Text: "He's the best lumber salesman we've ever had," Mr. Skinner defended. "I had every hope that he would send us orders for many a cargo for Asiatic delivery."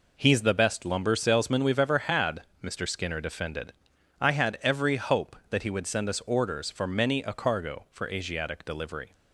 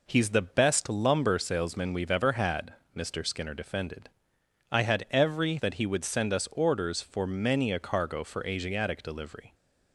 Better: first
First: none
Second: skips "hope"; at 5.5 s

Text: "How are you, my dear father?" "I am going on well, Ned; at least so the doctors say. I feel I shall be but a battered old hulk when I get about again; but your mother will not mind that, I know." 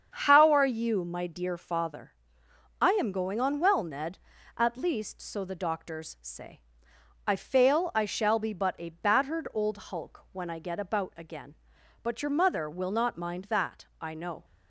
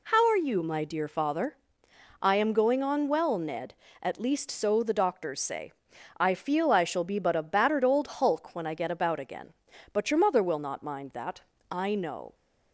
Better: second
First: starts louder than the rest; strong; until 1.1 s; 7.5 dB // says "fail" for "feel"; at 7.3 s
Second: none

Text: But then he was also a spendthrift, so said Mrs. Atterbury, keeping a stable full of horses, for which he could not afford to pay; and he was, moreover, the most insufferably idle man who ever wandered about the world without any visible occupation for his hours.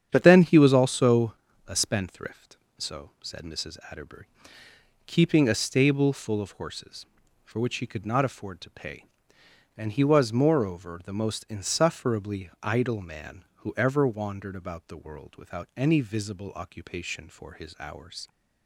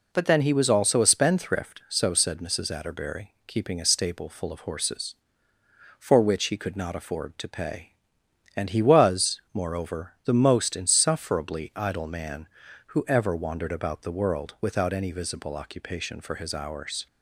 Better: second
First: starts louder than the rest; strong; until 1.1 s; 8.5 dB // changes voice at "then"; from 0.2 s on; 18.0 s long // pauses between "also" and "a"; slight; at 1.3 s; 0.32 s long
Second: none

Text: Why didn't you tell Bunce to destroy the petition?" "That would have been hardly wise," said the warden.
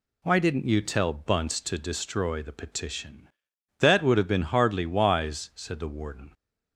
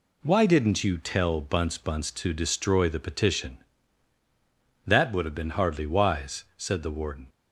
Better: first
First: none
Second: says "Bunce" twice; at 1.7 s

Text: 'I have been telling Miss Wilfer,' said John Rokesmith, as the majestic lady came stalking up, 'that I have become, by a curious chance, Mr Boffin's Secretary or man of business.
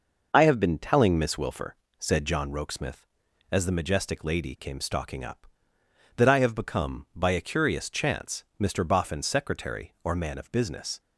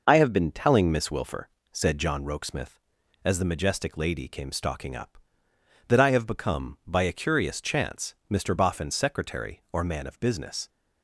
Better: neither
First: none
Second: none

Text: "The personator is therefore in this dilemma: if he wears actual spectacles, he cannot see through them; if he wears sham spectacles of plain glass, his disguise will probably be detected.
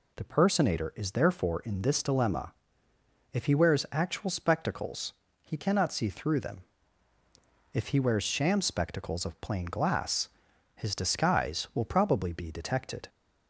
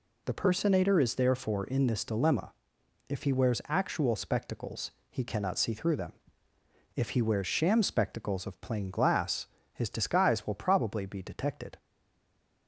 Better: first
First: none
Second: stays silent after the last word; slight; from 11.7 s on; 0.9 s long

